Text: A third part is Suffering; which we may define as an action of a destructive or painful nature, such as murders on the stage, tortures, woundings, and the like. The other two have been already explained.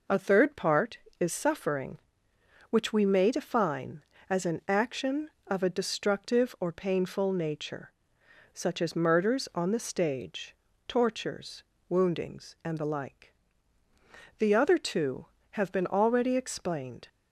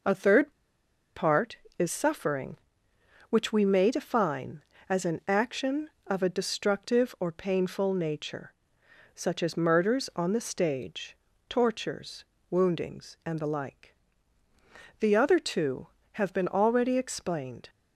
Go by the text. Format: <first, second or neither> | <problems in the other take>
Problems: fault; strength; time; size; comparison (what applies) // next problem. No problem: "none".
first | pauses between "third" and "part"; noticeable; at 0.5 s; 0.65 s long